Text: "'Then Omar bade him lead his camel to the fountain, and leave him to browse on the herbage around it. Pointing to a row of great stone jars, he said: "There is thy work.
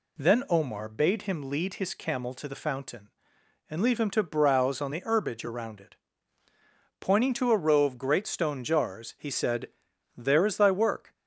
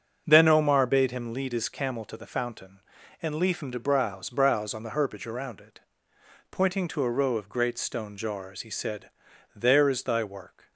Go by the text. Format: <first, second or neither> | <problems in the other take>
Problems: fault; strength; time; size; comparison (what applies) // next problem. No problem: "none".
first | starts louder than the rest; until 1.2 s; 6.5 dB // says "browse" twice; at 4.2 s